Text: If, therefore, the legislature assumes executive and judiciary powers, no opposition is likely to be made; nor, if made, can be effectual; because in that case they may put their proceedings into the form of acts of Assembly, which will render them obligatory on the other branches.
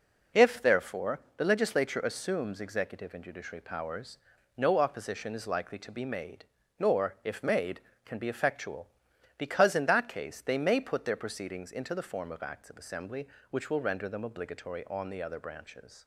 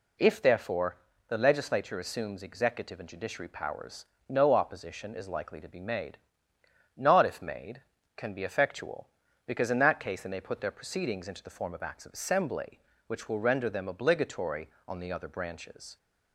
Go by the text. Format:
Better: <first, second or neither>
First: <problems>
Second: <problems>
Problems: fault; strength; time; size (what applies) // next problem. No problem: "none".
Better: first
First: none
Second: says "not" for "nor"; at 6.9 s